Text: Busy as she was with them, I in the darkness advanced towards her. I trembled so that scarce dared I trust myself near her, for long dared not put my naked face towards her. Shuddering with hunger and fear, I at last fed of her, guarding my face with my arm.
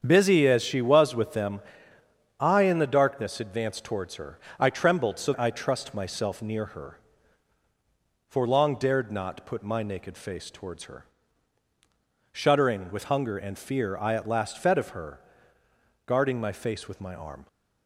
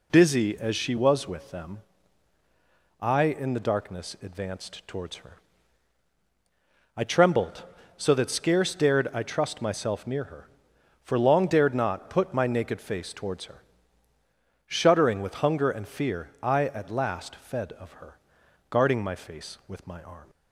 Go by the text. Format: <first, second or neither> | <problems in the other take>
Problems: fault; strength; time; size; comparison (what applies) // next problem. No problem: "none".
second | starts louder than the rest; strong; until 1.0 s; 7.5 dB // skips "that scarce dared"; at 5.3 s